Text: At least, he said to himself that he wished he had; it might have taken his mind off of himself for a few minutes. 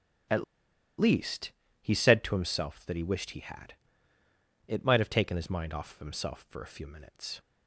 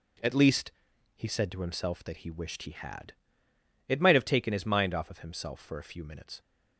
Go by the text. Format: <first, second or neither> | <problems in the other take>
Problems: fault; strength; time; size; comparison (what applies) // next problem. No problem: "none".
second | starts louder than the rest; strong; until 2.1 s; 10.5 dB // pauses between "At" and "least"; noticeable; at 0.4 s; 0.55 s long